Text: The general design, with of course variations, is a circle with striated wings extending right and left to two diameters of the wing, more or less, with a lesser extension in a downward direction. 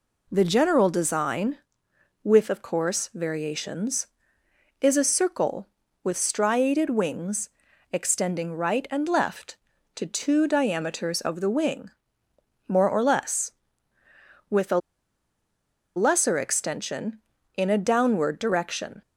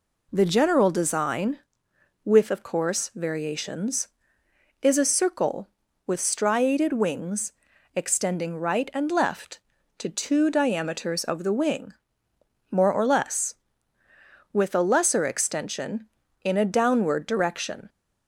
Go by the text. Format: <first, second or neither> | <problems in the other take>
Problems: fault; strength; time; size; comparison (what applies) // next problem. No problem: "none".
second | pauses between "wings" and "extending"; at 7.4 s; 0.44 s long; also in the second // pauses between "a" and "lesser"; at 14.7 s; 1.1 s long